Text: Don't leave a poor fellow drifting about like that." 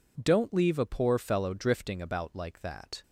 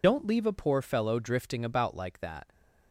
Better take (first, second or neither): first